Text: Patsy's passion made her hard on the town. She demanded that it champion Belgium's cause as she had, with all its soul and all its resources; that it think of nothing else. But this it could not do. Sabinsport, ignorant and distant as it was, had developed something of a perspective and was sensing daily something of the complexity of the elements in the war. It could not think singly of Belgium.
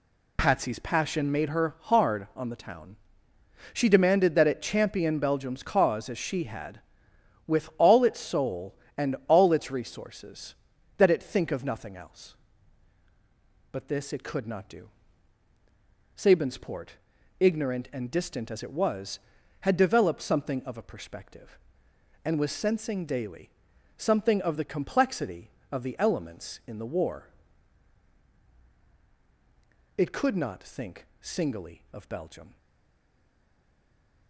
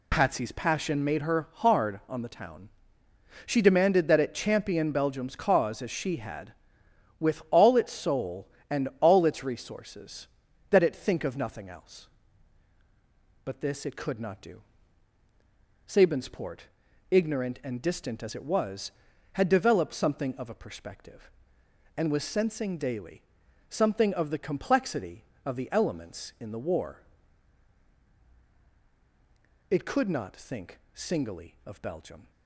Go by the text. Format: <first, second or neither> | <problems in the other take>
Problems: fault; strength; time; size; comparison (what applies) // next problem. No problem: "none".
second | pauses between "daily" and "something"; noticeable; at 23.4 s; 0.48 s long; noticeable in the second // stays silent after the last word; noticeable; from 32.5 s on; 1.7 s long